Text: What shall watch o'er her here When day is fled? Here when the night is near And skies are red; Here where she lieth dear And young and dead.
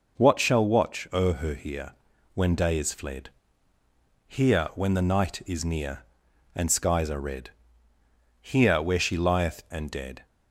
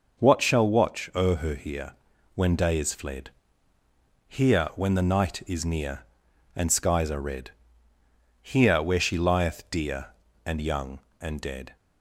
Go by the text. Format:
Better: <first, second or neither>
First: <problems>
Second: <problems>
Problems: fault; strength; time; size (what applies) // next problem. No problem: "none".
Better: second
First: pauses between "here" and "When"; at 1.9 s; 0.44 s long // skips "dear And young"; at 9.6 s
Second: pauses between "here" and "When"; at 1.9 s; 0.44 s long